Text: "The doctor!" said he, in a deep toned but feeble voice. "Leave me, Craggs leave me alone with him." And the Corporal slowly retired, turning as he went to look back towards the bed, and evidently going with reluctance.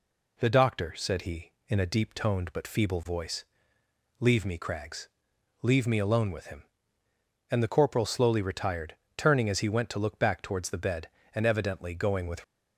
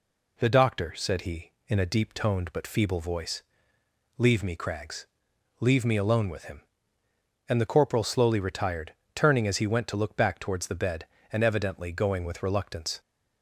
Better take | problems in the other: second | pauses between "Craggs" and "leave"; noticeable; at 5.0 s; 0.54 s long; noticeable in the second // stops before "reluctance"; at 12.4 s

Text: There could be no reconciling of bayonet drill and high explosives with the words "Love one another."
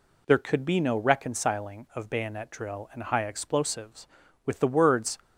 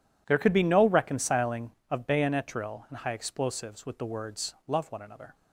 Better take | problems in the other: second | stops before "Love one another"; at 5.2 s

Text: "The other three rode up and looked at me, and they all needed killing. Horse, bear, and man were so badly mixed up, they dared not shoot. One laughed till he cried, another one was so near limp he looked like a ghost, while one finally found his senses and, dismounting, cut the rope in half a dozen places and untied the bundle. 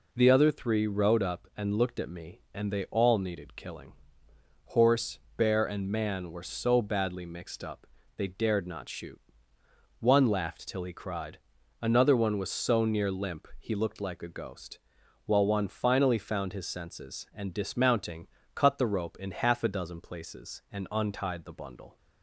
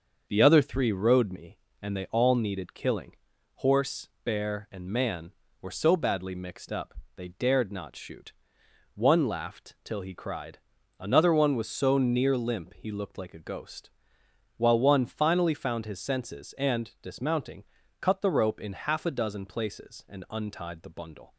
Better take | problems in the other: first | starts louder than the rest; until 1.3 s; 6.5 dB // skips "up and looked at"; at 1.3 s

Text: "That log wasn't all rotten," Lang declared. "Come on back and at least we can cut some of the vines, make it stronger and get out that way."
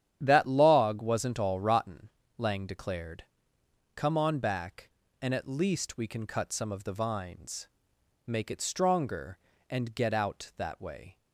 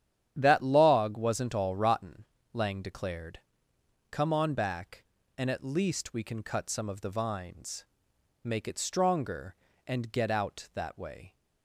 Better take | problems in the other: neither | starts louder than the rest; strong; the same in both

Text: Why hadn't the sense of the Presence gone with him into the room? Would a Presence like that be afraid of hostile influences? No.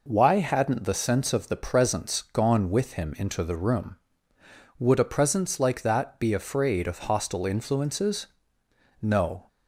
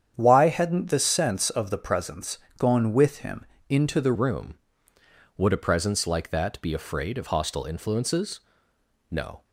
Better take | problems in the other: first | starts louder than the rest; strong; until 1.1 s; 8.5 dB // pauses between "Presence" and "gone"; slight; at 2.3 s; 0.20 s long // pauses between "him" and "into"; slight; at 3.4 s; 0.24 s long // changes voice at "room"; from 4.1 s on; 5.3 s long

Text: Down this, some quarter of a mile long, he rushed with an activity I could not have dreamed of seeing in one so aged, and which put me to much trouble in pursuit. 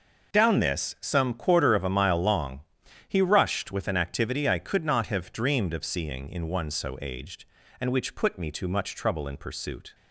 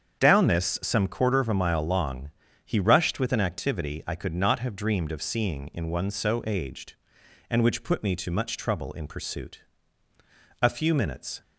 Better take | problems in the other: first | starts louder than the rest; strong; until 1.2 s; 7.5 dB // goes on to say "A few minutes"; noticeable; from 10.6 s on; 0.80 s long

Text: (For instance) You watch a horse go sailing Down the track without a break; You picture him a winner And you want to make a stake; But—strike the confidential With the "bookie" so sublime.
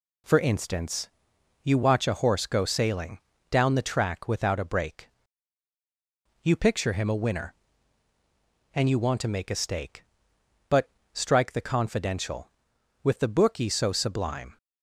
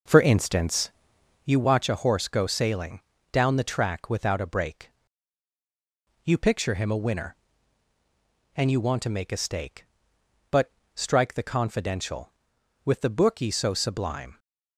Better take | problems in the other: first | starts louder than the rest; noticeable; until 1.6 s; 5.5 dB // pauses between "sailing" and "Down"; slight; at 3.0 s; 0.32 s long; slight in the first

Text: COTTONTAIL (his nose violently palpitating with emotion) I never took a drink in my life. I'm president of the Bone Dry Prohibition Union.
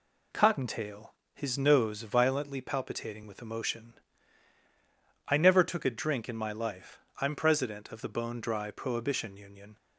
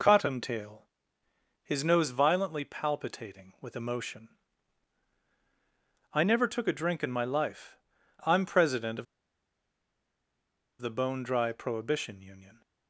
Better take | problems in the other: first | pauses between "of" and "the"; strong; at 9.0 s; 1.7 s long

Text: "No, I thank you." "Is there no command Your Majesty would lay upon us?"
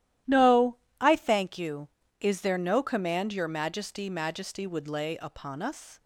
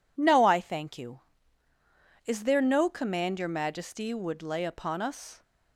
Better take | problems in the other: second | starts louder than the rest; strong; until 1.5 s; 13 dB // says "Majesty" twice; at 4.0 s

